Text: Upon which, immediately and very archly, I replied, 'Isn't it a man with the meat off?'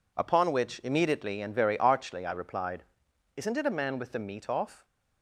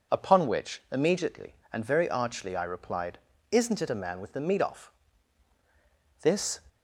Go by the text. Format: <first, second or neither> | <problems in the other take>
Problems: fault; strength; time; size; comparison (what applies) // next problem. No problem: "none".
first | goes on to say "This"; slight; from 6.2 s on; 0.38 s long